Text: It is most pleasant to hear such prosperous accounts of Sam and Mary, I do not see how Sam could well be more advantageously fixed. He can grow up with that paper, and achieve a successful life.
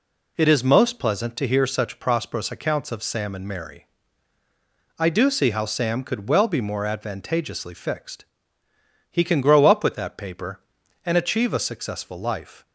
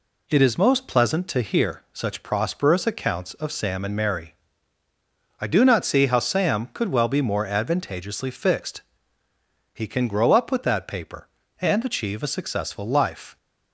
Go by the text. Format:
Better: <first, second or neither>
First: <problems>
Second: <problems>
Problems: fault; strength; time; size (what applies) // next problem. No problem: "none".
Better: second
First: skips "not"; at 5.2 s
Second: none